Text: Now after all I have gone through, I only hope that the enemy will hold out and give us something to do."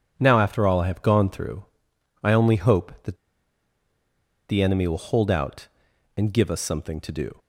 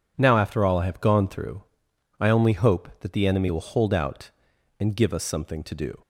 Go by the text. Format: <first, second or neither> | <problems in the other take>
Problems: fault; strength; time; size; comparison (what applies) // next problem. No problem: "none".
second | pauses between "that" and "the"; strong; at 3.1 s; 1.3 s long